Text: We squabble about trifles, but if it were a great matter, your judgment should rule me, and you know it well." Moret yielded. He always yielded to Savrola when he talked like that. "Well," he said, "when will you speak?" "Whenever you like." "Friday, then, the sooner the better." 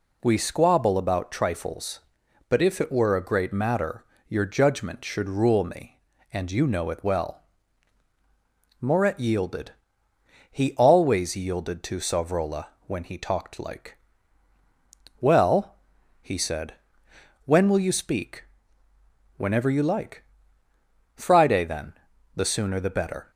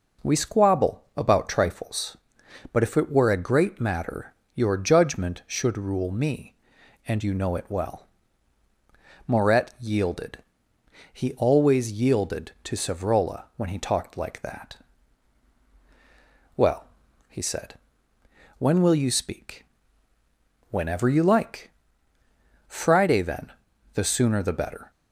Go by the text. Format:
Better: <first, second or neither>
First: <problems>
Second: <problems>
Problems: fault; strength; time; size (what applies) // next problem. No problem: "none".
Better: second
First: pauses between "Savrola" and "when"; slight; at 12.6 s; 0.20 s long // skips "that"; at 14.5 s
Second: none